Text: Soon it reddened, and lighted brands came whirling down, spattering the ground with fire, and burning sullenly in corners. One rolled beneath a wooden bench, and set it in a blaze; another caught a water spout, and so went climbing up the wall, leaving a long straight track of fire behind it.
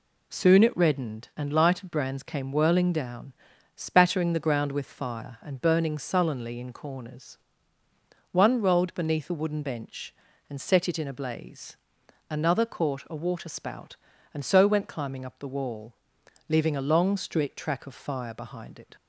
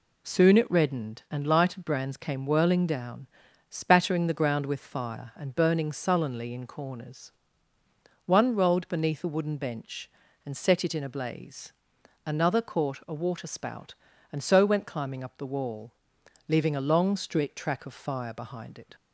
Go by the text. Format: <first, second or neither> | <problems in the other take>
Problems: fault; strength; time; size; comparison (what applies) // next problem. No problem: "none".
neither | none